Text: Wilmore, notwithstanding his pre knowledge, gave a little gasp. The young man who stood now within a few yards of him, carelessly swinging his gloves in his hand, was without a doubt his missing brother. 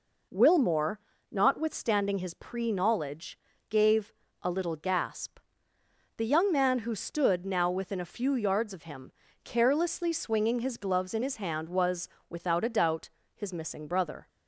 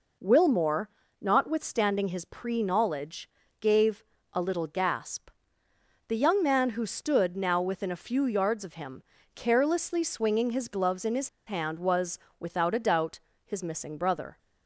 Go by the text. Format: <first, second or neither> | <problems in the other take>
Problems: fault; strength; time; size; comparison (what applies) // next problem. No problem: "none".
first | pauses between "gave" and "a"; slight; at 4.0 s; 0.28 s long; slight in the first // pauses between "his" and "hand"; slight; at 11.2 s; 0.18 s long // pauses between "was" and "without"; slight; at 12.1 s; 0.22 s long; slight in the first // pauses between "doubt" and "his"; slight; at 13.1 s; 0.26 s long; slight in the first